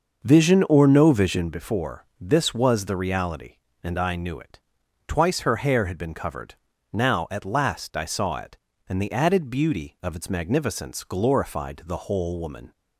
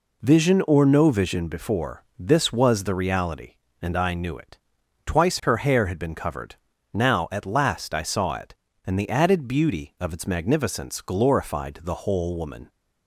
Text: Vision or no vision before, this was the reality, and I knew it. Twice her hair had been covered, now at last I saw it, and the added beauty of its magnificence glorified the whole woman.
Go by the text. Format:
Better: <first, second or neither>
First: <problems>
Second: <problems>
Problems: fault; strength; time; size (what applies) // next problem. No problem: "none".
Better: second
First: starts louder than the rest; until 1.5 s; 6.5 dB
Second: none